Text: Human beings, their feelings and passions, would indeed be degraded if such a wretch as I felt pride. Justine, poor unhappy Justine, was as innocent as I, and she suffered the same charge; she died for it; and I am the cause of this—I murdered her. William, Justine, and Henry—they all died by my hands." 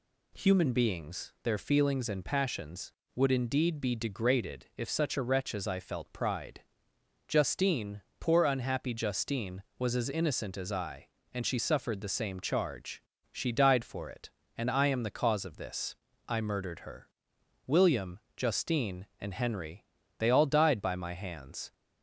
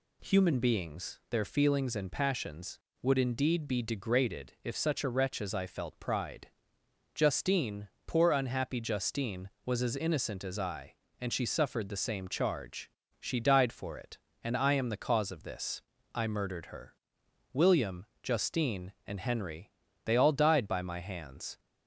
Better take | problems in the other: neither | none

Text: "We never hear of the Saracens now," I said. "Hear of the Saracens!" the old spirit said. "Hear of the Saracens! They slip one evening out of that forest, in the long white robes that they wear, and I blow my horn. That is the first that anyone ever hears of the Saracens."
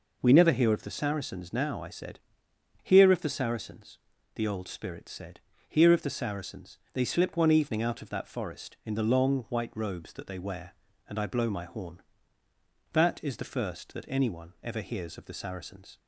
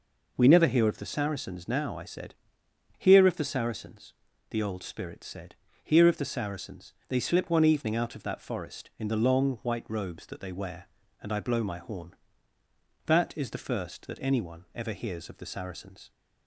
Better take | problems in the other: neither | none

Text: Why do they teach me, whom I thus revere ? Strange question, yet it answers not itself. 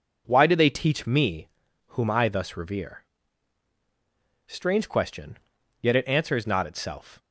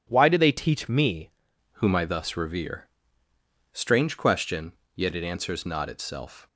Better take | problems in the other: first | changes voice at "whom"; from 1.7 s on; 4.7 s long

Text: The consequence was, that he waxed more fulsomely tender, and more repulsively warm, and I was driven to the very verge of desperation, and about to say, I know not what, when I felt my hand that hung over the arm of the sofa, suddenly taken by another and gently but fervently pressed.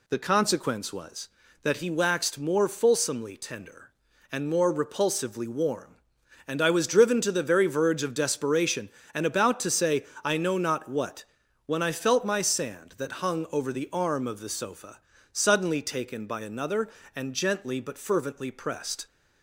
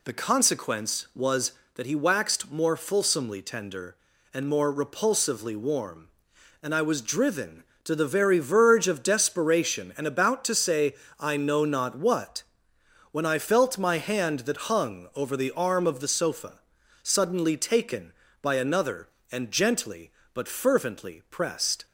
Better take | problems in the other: second | says "sand" for "hand"; at 12.4 s

